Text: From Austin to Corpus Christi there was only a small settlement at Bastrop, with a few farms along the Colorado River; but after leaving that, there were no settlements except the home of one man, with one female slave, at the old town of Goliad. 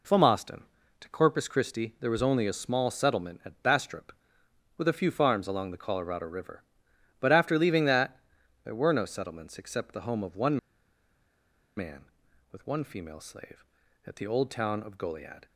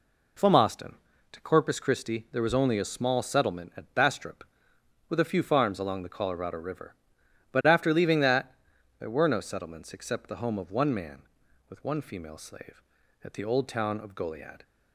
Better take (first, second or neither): second